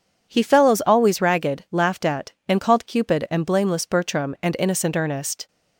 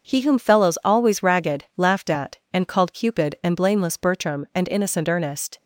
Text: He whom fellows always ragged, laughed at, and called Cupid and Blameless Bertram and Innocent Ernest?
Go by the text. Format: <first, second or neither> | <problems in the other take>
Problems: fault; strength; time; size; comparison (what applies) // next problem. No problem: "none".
second | skips "whom"; at 0.4 s